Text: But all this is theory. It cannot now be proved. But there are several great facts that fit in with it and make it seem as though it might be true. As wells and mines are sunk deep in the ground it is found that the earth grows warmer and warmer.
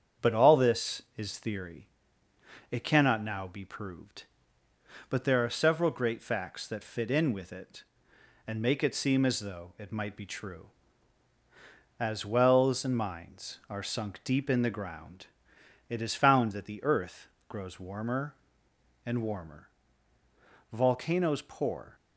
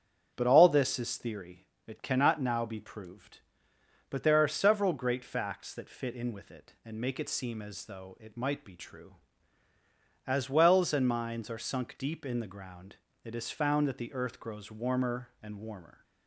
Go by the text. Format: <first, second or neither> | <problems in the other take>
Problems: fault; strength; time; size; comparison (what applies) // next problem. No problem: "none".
second | starts louder than the rest; strong; until 1.3 s; 7.5 dB; strong in the second // pauses between "ground" and "it"; noticeable; at 15.2 s; 0.62 s long; slight in the second // pauses between "earth" and "grows"; slight; at 17.2 s; 0.20 s long // goes on to say "Volcanoes pour"; noticeable; from 20.7 s on; 1.2 s long